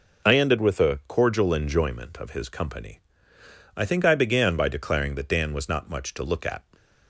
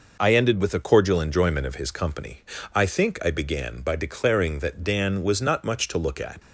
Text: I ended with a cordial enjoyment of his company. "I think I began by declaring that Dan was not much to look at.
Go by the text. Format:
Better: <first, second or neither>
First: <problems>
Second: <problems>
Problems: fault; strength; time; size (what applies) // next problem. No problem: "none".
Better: neither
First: none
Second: none